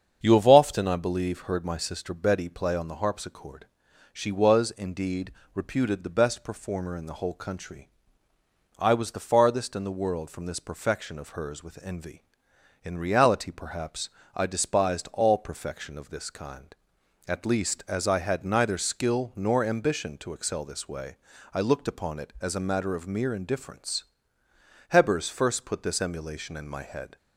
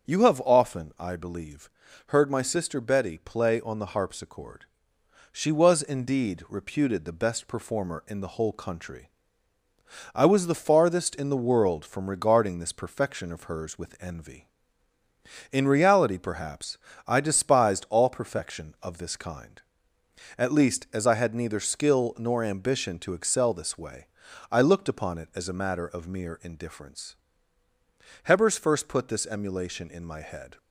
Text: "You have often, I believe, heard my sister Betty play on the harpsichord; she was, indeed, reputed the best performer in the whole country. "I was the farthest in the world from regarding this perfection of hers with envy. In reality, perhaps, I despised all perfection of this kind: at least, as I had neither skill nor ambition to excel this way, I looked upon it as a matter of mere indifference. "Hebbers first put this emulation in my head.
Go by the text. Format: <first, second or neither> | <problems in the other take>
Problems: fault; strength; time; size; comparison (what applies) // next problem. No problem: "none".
second | starts louder than the rest; strong; until 1.2 s; 7.5 dB; also in the second // skips "regarding"; at 10.4 s